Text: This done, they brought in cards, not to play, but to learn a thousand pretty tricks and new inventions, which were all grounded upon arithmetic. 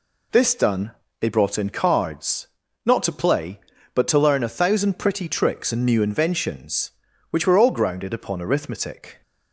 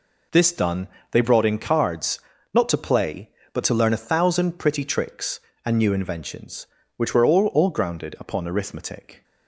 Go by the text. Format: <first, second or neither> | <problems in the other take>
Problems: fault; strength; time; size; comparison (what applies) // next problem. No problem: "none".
first | says "all" twice; at 7.4 s